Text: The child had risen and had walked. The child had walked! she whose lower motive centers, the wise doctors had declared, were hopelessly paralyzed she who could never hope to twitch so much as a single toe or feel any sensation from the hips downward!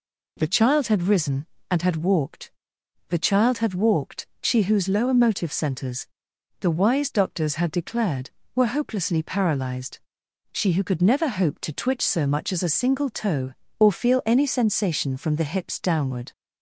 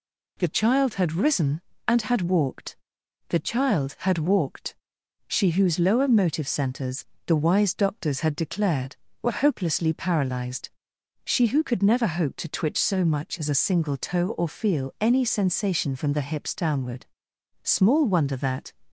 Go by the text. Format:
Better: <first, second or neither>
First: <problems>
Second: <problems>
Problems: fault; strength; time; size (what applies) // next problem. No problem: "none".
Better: first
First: pauses between "paralyzed" and "she"; noticeable; at 9.9 s; 0.54 s long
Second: pauses between "paralyzed" and "she"; noticeable; at 10.6 s; 0.54 s long // goes on to say "Small wonder that"; noticeable; from 17.6 s on; 1.1 s long